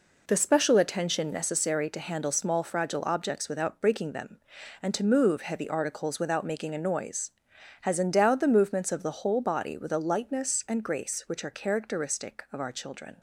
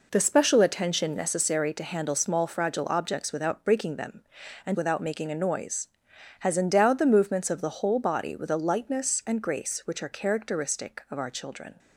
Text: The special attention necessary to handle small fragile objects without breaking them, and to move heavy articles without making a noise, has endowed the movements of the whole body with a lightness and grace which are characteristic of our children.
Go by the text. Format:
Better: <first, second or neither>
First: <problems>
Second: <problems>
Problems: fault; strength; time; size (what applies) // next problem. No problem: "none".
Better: first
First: none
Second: skips "to move heavy articles"; at 4.7 s